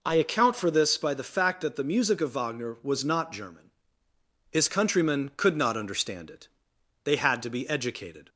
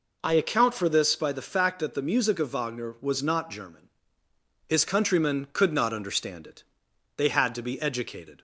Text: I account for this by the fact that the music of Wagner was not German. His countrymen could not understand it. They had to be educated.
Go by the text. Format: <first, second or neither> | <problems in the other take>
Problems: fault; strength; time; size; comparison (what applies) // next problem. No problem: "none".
neither | none